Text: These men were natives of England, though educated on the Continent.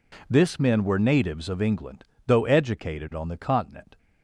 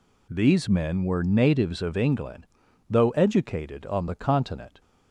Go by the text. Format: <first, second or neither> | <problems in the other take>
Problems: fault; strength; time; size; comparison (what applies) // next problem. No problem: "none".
second | says "This" for "These"; at 0.2 s